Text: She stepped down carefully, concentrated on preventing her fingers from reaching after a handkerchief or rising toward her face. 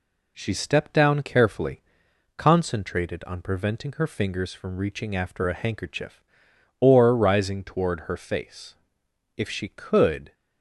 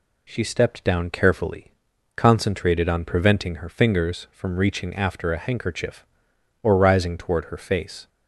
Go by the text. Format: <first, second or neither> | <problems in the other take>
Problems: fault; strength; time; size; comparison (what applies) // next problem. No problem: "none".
second | goes on to say "If she could"; noticeable; from 9.3 s on; 0.96 s long